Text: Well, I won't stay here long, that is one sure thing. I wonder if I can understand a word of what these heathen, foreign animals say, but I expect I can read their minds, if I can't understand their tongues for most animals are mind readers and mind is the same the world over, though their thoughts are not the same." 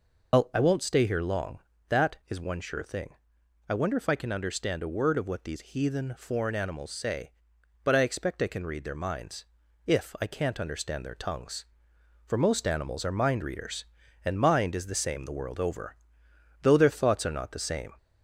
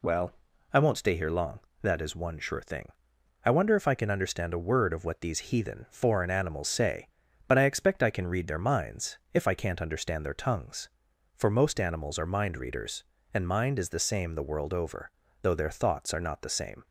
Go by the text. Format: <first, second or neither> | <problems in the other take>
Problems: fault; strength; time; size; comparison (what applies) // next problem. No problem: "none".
second | loses the start of "Well"; at 0.3 s; 115 ms